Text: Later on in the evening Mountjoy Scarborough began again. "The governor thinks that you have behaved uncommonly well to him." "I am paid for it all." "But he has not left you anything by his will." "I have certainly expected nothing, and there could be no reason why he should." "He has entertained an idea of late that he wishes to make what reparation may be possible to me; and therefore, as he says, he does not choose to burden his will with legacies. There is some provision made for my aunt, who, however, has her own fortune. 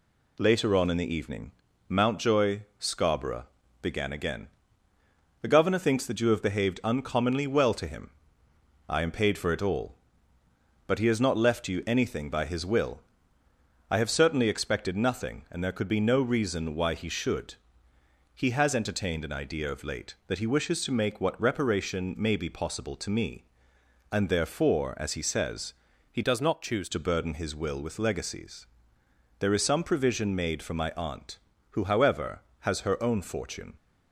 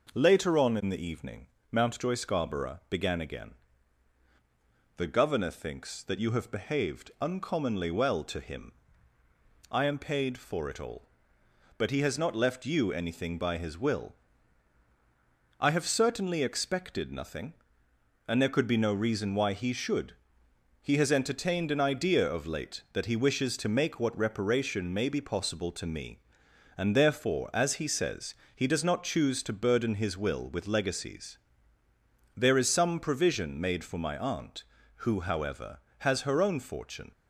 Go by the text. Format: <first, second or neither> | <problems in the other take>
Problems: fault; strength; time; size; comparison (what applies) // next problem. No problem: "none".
second | pauses between "evening" and "Mountjoy"; slight; at 1.5 s; 0.36 s long; slight in the second // pauses between "Mountjoy" and "Scarborough"; slight; at 2.6 s; 0.18 s long // pauses between "Scarborough" and "began"; slight; at 3.4 s; 0.36 s long // changes voice from "does" to "choose"; from 26.2 to 26.8 s; 0.6 s long